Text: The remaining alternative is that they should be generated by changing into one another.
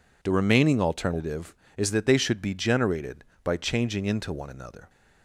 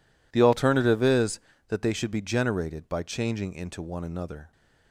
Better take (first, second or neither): first